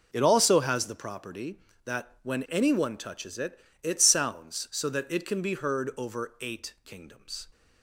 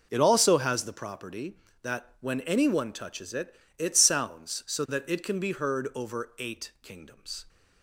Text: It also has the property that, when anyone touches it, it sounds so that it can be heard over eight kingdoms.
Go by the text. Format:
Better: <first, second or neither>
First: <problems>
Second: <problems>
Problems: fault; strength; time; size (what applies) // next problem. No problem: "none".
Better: neither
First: none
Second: none